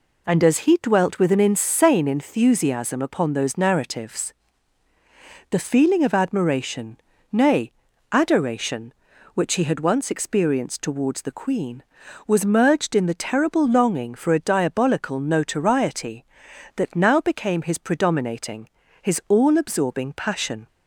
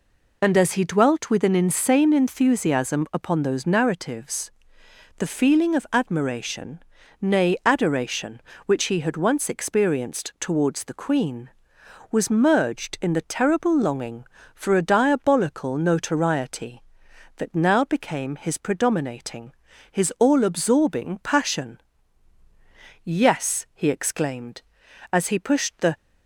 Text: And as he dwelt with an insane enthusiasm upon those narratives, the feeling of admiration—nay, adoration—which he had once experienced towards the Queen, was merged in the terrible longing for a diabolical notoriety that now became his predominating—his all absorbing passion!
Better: first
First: none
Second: goes on to say "Yes he exclaimed as he pushed the"; strong; from 23.0 s on; 2.9 s long

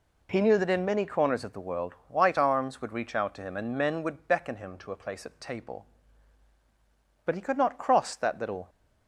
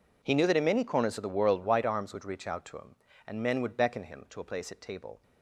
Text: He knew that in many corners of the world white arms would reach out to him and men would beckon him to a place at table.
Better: second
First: goes on to say "But he could not cross that little"; from 7.2 s on; 1.4 s long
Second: none

